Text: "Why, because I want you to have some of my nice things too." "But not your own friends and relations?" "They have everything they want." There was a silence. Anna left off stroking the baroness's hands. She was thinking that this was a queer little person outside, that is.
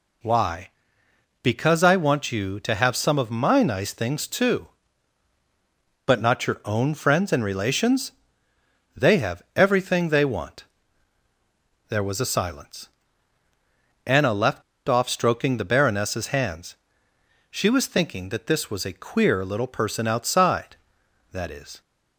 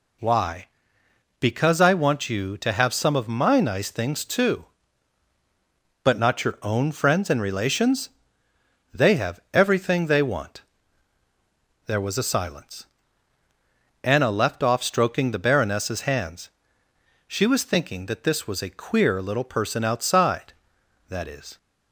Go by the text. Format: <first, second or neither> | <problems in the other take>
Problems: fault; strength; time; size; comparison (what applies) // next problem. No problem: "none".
second | pauses between "left" and "off"; slight; at 14.6 s; 0.24 s long